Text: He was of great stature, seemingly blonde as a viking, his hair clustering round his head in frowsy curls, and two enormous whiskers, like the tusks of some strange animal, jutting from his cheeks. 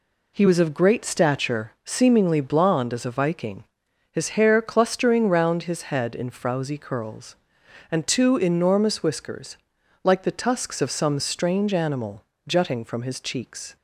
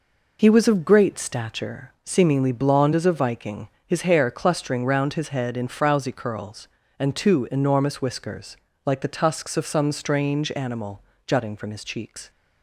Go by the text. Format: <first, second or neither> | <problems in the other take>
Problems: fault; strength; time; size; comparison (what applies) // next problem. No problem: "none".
neither | none